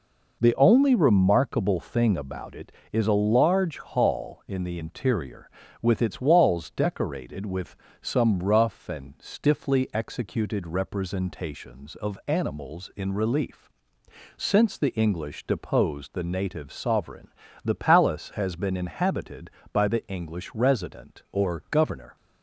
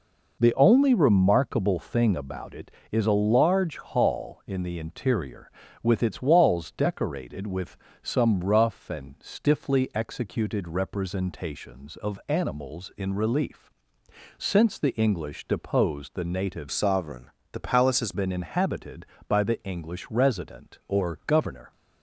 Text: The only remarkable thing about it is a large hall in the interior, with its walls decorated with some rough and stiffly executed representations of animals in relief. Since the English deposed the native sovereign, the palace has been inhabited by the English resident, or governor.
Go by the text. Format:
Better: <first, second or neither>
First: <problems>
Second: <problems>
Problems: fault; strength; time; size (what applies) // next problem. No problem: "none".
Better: first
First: pauses between "with" and "some"; slight; at 7.7 s; 0.28 s long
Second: pauses between "with" and "some"; slight; at 7.7 s; 0.28 s long // changes voice from "sovereign" to "has"; from 16.7 to 18.1 s; 1.4 s long